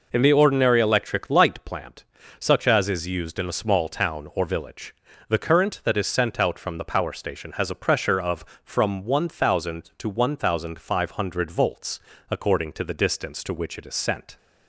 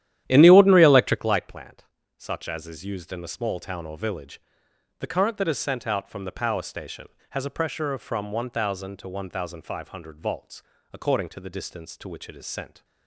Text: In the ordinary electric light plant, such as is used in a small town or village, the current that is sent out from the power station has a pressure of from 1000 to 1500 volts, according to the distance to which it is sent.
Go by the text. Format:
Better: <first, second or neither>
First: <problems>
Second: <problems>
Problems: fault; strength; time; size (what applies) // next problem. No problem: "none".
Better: first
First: none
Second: starts louder than the rest; strong; until 1.3 s; 11.5 dB